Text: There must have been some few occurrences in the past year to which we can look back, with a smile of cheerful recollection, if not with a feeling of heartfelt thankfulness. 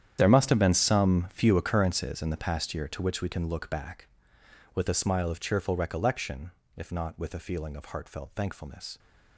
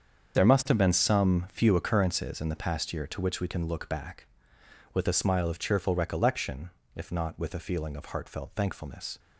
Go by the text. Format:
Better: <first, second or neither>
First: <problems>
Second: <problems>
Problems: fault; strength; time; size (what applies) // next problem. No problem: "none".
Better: second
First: gets quieter; strong; throughout; 16 dB // starts louder than the rest; strong; until 1.2 s; 9.5 dB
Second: starts louder than the rest; until 1.4 s; 7 dB